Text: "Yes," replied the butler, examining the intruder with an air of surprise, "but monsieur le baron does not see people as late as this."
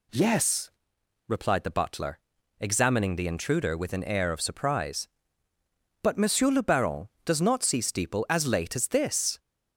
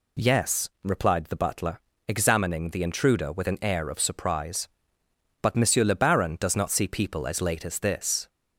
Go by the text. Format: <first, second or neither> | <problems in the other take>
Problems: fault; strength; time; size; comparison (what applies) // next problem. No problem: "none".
second | says "steeple" for "people"; at 7.8 s